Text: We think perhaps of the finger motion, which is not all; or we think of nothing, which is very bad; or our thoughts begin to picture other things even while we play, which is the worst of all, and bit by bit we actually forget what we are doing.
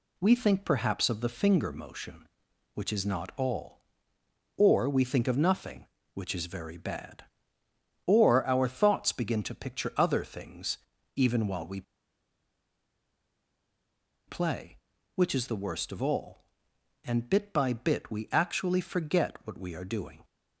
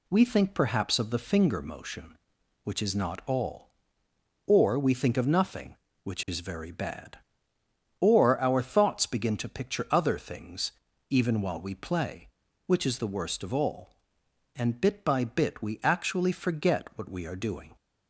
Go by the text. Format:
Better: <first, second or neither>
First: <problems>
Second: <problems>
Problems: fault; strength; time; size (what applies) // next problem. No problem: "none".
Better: second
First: pauses between "things" and "even"; at 10.7 s; 0.38 s long // pauses between "we" and "play"; strong; at 11.8 s; 2.4 s long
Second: pauses between "things" and "even"; at 10.7 s; 0.38 s long